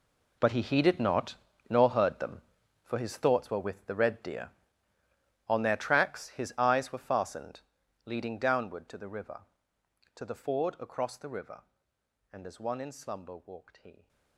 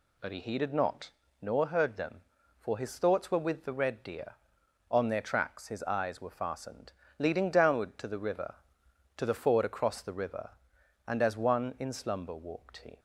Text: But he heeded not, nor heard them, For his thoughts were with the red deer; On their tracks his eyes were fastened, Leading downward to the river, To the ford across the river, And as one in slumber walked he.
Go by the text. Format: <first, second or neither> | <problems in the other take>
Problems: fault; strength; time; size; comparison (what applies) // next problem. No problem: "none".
second | gets quieter; strong; throughout; 15.5 dB